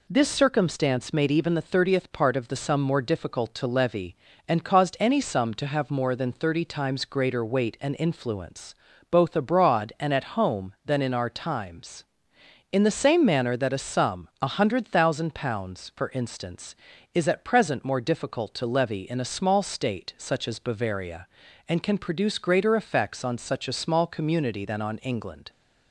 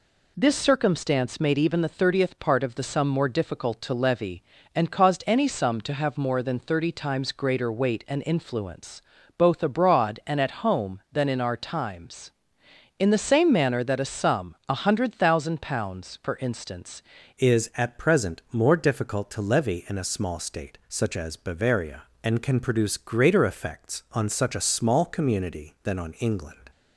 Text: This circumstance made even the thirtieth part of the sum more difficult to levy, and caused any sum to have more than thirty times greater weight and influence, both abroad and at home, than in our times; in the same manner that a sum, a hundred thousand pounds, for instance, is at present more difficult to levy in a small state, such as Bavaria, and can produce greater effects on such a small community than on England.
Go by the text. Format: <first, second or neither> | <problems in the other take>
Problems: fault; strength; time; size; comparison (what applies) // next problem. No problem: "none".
first | changes voice at "is"; from 17.3 s on; 9.4 s long